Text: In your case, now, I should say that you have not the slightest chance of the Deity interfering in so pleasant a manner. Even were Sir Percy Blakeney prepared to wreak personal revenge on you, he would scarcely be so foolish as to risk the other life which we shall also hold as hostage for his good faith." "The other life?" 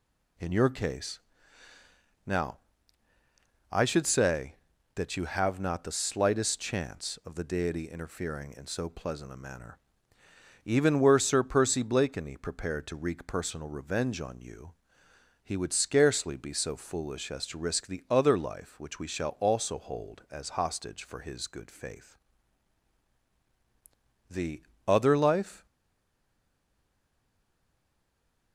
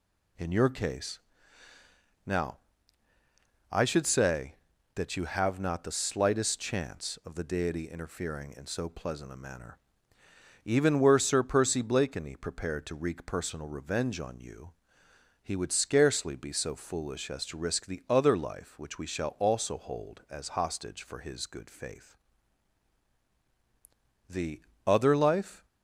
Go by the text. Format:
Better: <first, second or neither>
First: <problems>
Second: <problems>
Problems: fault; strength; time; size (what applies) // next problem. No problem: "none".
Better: second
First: pauses between "The" and "other"; slight; at 24.6 s; 0.22 s long // stays silent after the last word; strong; from 25.6 s on; 2.9 s long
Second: pauses between "The" and "other"; slight; at 24.6 s; 0.22 s long